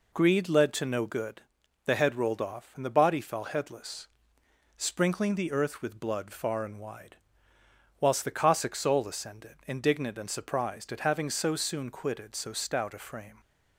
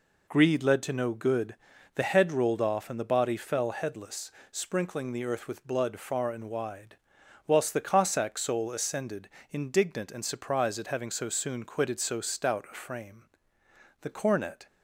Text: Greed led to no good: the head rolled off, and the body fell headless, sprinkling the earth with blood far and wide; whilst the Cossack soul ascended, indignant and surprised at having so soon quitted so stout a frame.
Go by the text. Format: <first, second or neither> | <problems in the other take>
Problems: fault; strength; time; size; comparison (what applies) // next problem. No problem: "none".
first | goes on to say "The cornet"; noticeable; from 14.0 s on; 0.64 s long